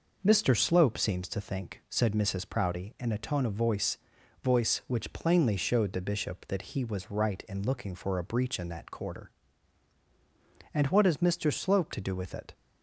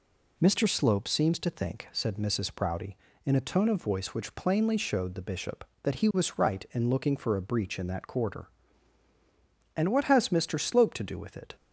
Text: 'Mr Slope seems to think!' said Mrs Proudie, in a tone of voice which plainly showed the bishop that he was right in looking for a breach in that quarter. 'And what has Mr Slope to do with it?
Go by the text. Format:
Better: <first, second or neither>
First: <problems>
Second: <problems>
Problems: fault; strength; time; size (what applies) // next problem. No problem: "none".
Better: second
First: says "voice" twice; at 4.4 s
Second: none